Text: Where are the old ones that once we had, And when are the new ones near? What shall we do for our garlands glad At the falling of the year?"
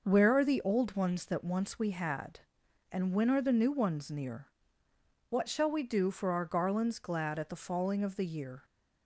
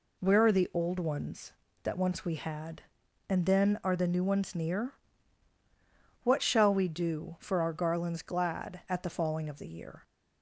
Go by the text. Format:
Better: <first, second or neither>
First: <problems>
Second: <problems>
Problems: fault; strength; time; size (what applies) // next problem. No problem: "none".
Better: first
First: none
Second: says "then" for "when"; at 3.4 s